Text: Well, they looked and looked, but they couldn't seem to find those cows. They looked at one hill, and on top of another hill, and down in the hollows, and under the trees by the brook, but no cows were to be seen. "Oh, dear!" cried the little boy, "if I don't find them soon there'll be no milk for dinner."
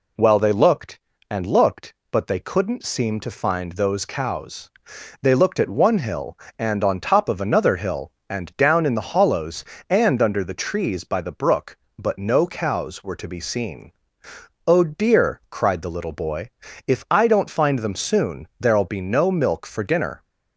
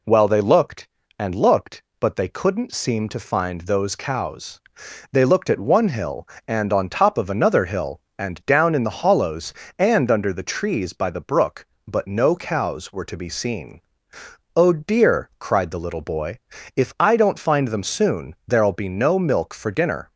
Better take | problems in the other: neither | none

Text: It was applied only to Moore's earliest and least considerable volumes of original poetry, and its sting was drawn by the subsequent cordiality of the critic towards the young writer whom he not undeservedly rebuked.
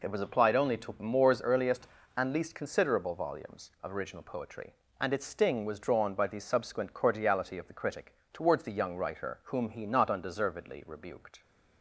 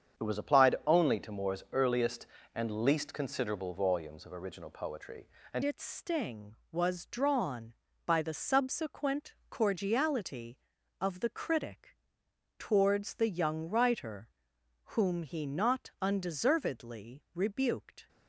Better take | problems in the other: first | starts louder than the rest; strong; until 1.2 s; 7.5 dB // changes voice at "its"; from 5.6 s on; 12.4 s long // pauses between "critic" and "towards"; noticeable; at 11.9 s; 0.62 s long; slight in the first // pauses between "writer" and "whom"; noticeable; at 14.2 s; 0.66 s long

